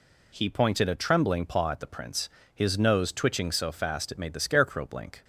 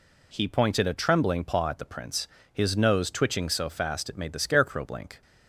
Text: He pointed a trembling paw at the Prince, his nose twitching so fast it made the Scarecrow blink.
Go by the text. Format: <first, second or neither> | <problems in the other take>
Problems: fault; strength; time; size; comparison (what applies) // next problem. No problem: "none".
neither | none